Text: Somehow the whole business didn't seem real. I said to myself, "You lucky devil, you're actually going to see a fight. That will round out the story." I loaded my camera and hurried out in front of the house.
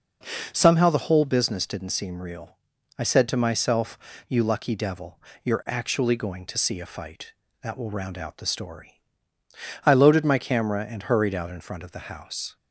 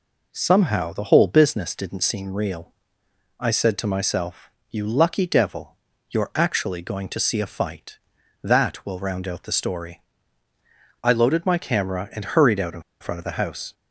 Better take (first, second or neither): first